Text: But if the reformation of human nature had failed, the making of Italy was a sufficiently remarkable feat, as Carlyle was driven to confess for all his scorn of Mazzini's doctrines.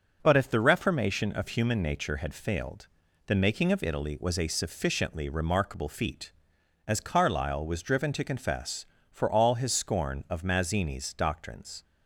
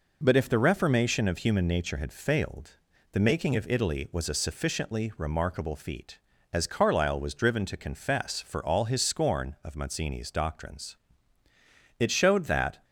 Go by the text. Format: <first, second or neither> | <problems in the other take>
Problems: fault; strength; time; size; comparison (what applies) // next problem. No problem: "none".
first | goes on to say "It showed that"; noticeable; from 11.9 s on; 0.86 s long